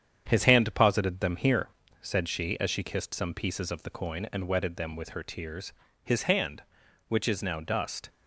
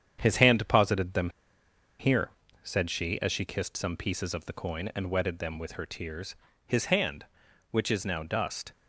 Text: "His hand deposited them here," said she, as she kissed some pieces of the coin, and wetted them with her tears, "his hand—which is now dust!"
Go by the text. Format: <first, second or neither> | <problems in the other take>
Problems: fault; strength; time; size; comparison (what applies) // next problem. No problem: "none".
first | starts louder than the rest; strong; until 1.2 s; 8.5 dB; strong in the first // pauses between "them" and "here"; noticeable; at 1.2 s; 0.70 s long